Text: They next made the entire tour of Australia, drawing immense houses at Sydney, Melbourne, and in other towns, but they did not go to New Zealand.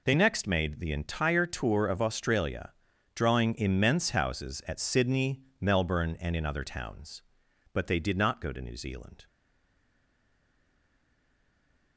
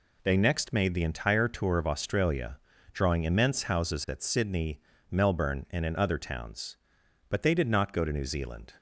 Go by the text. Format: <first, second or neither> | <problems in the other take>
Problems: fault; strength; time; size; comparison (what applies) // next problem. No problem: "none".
second | stays silent after the last word; strong; from 9.2 s on; 2.7 s long